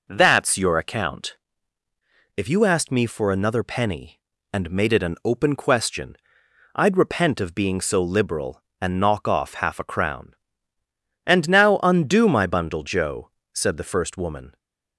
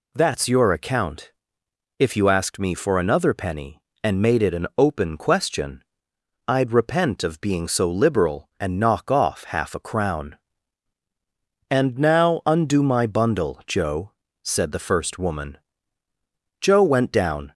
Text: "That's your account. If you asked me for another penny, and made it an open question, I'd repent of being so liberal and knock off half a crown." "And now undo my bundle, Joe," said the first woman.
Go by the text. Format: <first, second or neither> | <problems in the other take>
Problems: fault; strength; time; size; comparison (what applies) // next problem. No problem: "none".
first | goes on to say "Joe went down"; noticeable; from 16.5 s on; 0.94 s long